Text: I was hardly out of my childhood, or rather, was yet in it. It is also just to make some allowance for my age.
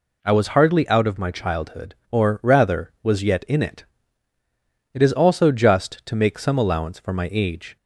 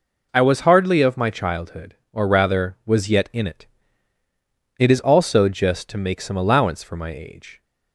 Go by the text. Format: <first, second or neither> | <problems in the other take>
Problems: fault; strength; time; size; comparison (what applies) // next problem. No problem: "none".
first | skips "out"; at 1.0 s